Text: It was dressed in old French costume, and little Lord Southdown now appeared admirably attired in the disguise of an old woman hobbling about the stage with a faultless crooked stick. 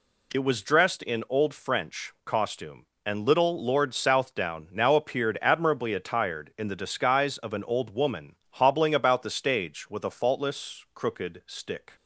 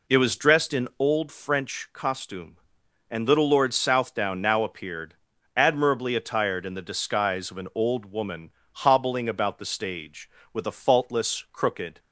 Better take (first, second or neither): first